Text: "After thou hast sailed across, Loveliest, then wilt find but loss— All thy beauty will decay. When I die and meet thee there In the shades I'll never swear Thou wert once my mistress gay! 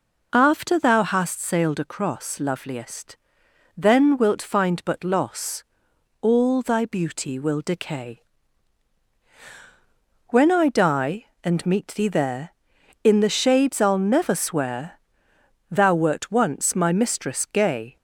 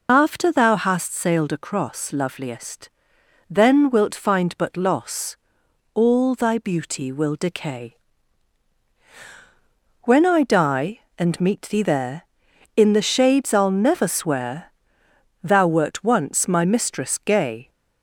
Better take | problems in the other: first | loses the start of "After"; at 0.0 s; 50 ms // pauses between "swear" and "Thou"; noticeable; at 14.7 s; 0.72 s long; noticeable in the first

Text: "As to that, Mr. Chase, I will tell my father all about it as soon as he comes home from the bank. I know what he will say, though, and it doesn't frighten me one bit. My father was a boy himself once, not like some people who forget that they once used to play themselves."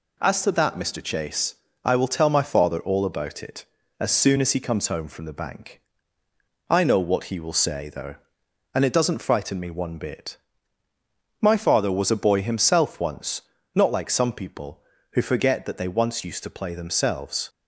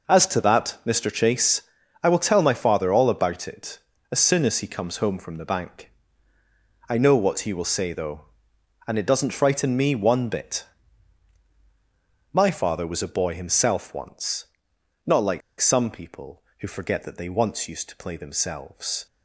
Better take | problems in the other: first | pauses between "like" and "some"; slight; at 15.4 s; 0.19 s long

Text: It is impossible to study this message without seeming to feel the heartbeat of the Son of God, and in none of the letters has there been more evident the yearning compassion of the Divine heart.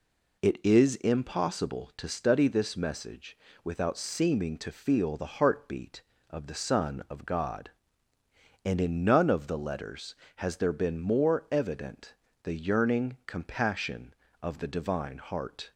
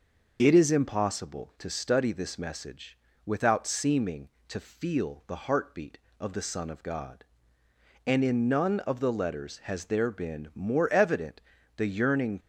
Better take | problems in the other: first | pauses between "message" and "without"; slight; at 2.9 s; 0.30 s long; slight in the first // pauses between "evident" and "the"; slight; at 11.4 s; 0.36 s long; slight in the first // stops before "compassion of the Divine heart"; at 12.3 s

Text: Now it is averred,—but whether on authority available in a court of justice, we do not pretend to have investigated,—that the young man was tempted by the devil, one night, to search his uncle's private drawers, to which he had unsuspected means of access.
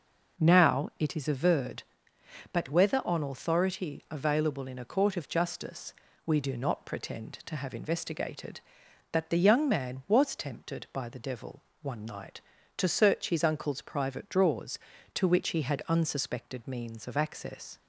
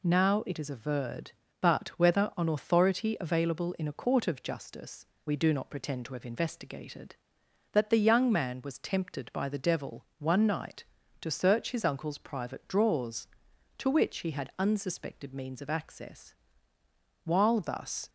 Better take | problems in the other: first | goes on to say "While thus"; noticeable; from 17.2 s on; 0.84 s long

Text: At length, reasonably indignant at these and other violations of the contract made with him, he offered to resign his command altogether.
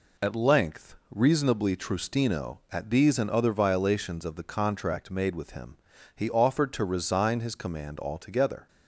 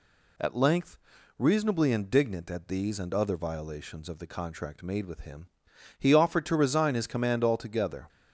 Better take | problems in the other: second | says "trustino" for "indignant"; at 1.7 s

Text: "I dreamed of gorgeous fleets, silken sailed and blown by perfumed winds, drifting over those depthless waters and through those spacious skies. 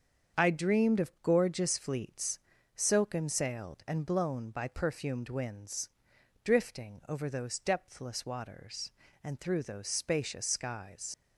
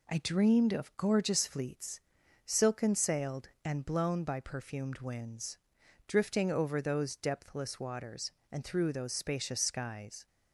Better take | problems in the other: second | starts louder than the rest; strong; until 1.4 s; 7 dB // leaves "skies" unfinished; at 11.1 s; 80 ms

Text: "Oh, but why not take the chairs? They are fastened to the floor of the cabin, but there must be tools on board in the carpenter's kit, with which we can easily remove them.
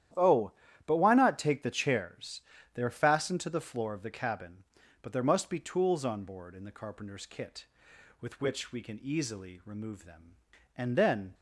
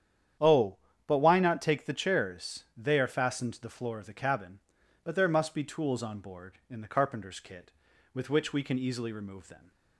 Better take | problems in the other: second | starts louder than the rest; strong; until 1.5 s; 11 dB; strong in the second // goes on to say "And then"; from 10.7 s on; 0.58 s long

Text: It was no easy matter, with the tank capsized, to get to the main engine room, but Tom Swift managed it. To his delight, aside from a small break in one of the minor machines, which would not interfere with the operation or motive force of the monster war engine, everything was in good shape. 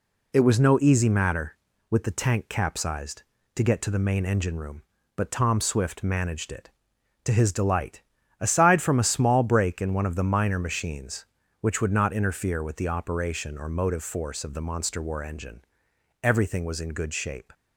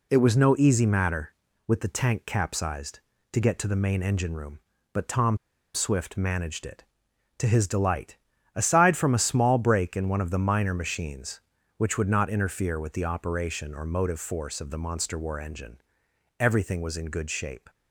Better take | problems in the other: first | pauses between "Tom" and "Swift"; at 5.3 s; 0.38 s long

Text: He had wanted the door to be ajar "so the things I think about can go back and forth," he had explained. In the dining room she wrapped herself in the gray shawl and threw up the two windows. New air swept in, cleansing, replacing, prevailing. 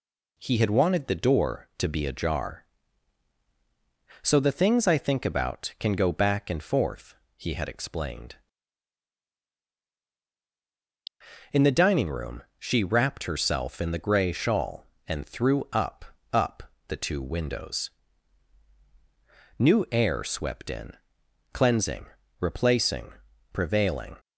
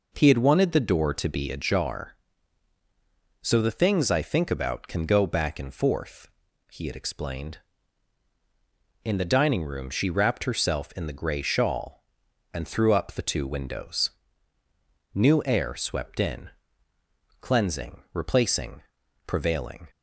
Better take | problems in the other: second | pauses between "room" and "she"; slight; at 12.4 s; 0.16 s long // says "up" twice; at 16.3 s

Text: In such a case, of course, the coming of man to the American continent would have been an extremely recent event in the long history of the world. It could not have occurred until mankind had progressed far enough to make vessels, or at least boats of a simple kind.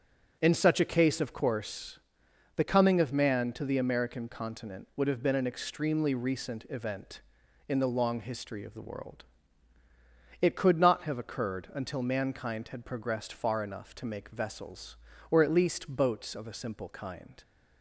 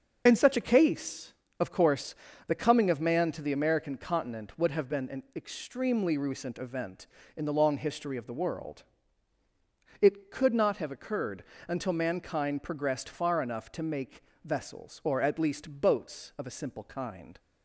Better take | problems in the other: first | starts louder than the rest; until 1.2 s; 6.5 dB; also in the first // pauses between "occurred" and "until"; slight; at 11.4 s; 0.24 s long // skips "had"; at 12.6 s // pauses between "make" and "vessels"; slight; at 14.2 s; 0.22 s long

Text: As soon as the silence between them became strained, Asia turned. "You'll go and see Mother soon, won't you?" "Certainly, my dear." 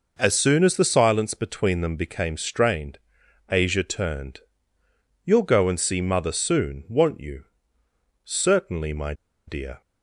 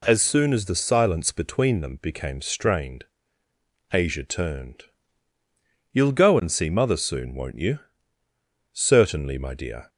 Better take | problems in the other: second | pauses between "my" and "dear"; slight; at 9.1 s; 0.34 s long

